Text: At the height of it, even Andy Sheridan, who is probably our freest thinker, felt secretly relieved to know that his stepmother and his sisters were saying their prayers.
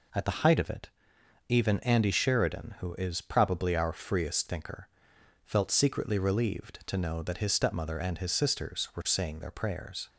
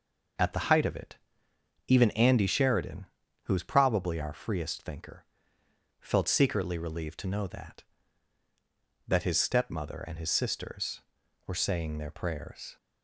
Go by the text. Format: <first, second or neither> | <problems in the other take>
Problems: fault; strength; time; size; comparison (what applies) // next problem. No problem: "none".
first | says "that" twice; at 9.0 s